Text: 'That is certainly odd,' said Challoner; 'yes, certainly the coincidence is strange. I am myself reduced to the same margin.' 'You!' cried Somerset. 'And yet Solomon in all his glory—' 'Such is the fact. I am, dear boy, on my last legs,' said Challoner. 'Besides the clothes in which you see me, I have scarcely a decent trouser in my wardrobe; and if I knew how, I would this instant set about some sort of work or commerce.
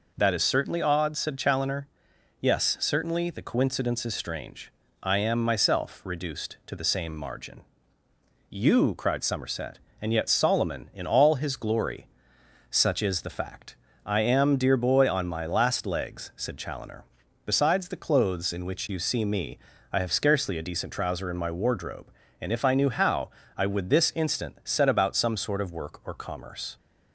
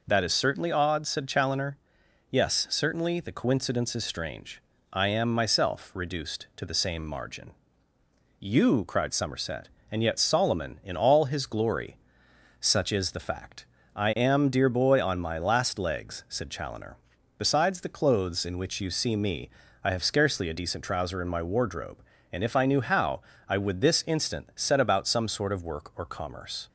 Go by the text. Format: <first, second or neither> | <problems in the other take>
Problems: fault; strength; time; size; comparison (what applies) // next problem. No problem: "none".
neither | none